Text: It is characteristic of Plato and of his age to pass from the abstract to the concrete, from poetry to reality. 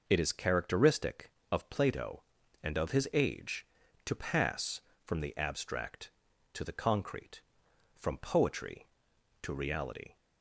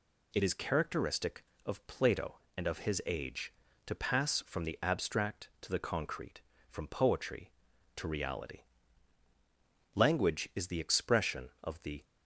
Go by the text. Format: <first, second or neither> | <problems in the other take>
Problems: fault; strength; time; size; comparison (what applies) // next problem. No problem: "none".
first | goes on to say "Language is the expression of the"; strong; from 9.9 s on; 2.1 s long